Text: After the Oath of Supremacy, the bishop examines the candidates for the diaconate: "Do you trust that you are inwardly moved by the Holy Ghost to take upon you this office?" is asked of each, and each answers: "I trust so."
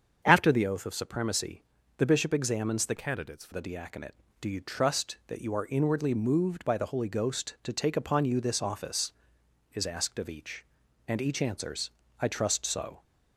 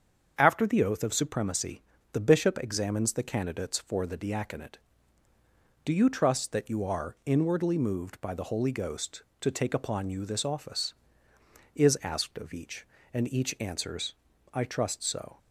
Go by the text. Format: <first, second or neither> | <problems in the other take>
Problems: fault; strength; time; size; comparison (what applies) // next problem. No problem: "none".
second | starts louder than the rest; strong; until 1.2 s; 7 dB; also in the second // changes voice from "candidates" to "for"; from 2.9 to 3.5 s; 0.6 s long